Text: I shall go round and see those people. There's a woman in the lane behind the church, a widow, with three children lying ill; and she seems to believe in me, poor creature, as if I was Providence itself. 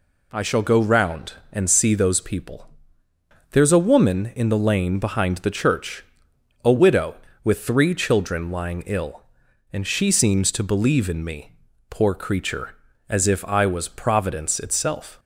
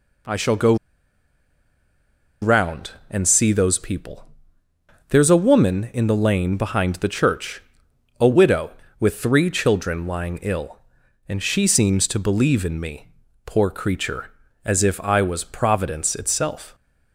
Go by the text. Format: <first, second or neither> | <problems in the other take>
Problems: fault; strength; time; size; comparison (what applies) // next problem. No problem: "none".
first | pauses between "go" and "round"; strong; at 0.7 s; 1.6 s long